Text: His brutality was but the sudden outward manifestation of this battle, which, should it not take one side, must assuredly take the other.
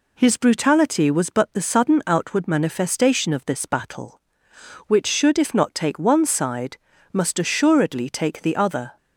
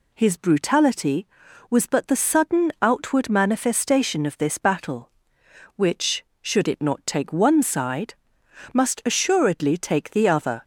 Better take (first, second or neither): second